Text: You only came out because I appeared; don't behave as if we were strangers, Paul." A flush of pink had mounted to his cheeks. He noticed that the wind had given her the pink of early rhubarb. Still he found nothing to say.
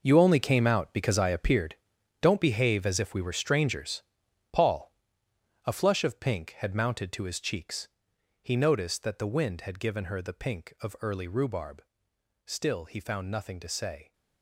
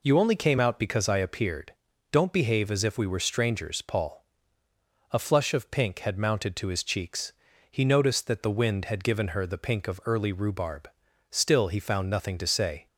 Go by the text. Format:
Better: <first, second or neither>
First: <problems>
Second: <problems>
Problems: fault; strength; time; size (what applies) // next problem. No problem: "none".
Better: second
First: gets quieter; strong; throughout; 12 dB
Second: none